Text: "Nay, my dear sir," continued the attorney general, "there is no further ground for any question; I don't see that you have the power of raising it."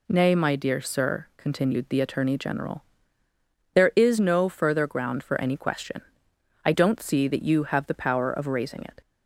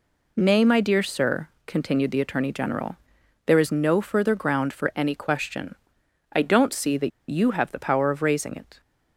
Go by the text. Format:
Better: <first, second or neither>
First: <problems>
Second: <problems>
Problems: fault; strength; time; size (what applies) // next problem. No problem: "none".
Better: first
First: none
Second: pauses between "that" and "you"; slight; at 7.1 s; 0.20 s long